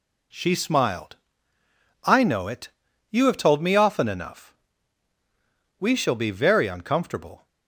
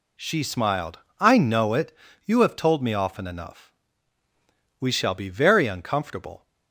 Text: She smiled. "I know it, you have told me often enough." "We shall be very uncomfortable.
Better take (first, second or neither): neither